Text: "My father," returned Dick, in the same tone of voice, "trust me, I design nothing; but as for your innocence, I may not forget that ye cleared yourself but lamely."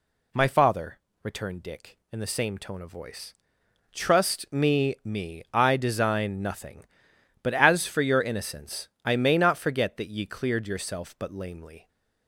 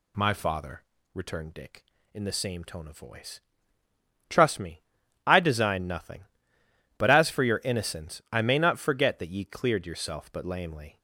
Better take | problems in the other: second | says "me" twice; at 5.0 s

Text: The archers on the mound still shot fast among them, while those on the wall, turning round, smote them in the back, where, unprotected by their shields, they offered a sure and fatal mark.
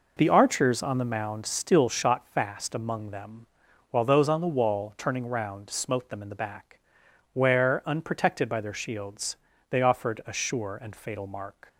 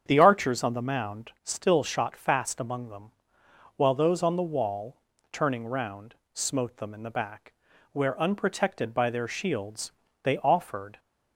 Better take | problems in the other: first | starts louder than the rest; strong; until 1.0 s; 7.5 dB // stops before "a sure and fatal mark"; at 10.9 s

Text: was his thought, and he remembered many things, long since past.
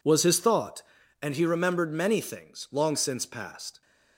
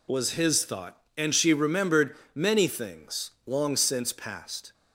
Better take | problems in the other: first | says "she" for "he"; at 1.3 s // pauses between "remembered" and "many"; slight; at 2.1 s; 0.20 s long

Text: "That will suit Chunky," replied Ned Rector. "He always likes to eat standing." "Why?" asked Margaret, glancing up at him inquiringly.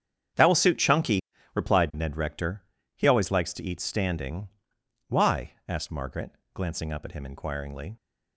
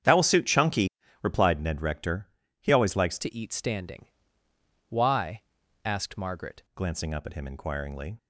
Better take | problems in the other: first | starts louder than the rest; strong; until 1.3 s; 8.5 dB; strong in the first // changes voice from "to" to "Margaret"; from 3.1 to 6.6 s; 3.5 s long

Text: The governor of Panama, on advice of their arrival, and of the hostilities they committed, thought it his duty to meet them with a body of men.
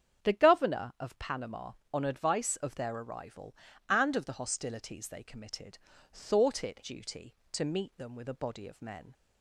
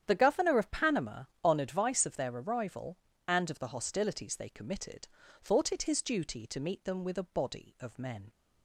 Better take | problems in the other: second | starts louder than the rest; strong; until 1.3 s; 8 dB; strong in the second // skips "his"; at 6.8 s

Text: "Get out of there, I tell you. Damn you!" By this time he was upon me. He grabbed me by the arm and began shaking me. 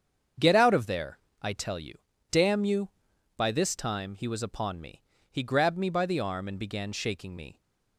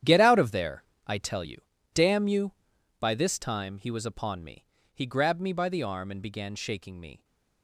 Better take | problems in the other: first | gets quieter; strong; throughout; 14 dB // starts louder than the rest; strong; until 1.2 s; 10 dB; strong in the first

